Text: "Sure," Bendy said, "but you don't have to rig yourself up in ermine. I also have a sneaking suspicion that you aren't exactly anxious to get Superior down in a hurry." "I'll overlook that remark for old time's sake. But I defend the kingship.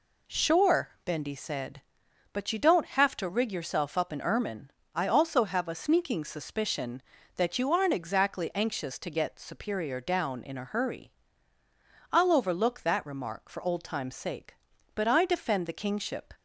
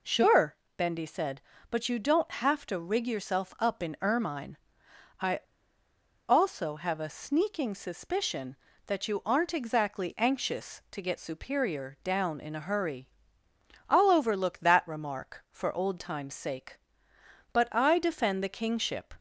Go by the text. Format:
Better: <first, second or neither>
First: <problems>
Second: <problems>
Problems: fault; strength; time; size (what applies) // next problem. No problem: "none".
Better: first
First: none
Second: pauses between "I" and "also"; noticeable; at 5.3 s; 0.89 s long